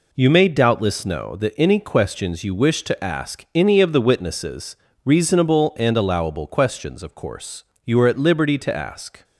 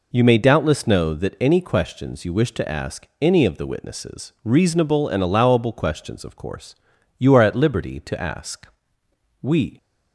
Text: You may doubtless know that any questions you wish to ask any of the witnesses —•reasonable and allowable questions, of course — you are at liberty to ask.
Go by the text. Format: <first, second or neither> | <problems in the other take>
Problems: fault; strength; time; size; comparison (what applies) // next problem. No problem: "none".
first | goes on to say "We"; slight; from 9.4 s on; 0.36 s long